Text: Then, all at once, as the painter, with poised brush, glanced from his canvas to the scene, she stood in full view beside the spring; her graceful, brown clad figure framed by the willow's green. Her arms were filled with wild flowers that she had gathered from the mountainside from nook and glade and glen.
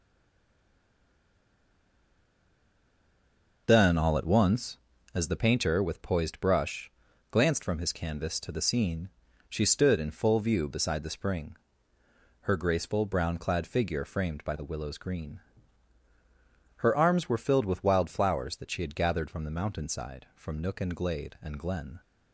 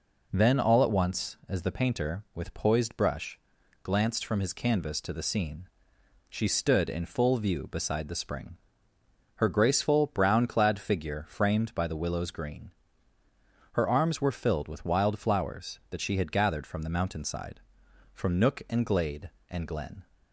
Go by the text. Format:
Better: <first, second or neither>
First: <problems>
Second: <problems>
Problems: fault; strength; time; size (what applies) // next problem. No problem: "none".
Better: second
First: stays silent before the first word; strong; until 3.6 s; 3.6 s long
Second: none